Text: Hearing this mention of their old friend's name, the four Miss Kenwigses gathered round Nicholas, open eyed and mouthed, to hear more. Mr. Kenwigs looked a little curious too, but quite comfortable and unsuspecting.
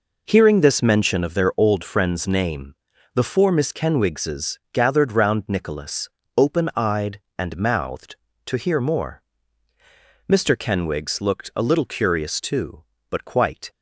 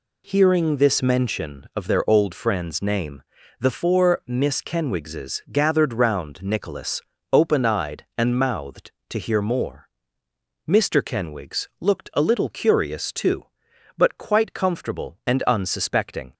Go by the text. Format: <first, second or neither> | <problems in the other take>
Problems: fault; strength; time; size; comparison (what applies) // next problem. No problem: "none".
second | stops before "comfortable and unsuspecting"; at 13.6 s